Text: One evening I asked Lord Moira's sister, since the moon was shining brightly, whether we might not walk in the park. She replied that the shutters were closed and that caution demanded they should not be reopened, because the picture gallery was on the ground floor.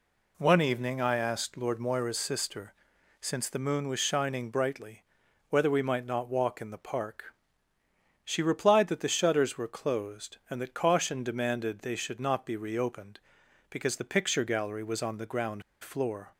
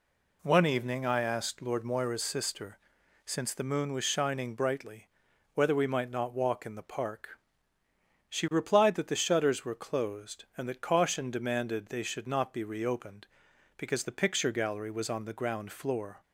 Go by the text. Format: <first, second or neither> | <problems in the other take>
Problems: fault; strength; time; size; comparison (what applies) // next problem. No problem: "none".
second | pauses between "ground" and "floor"; slight; at 15.6 s; 0.19 s long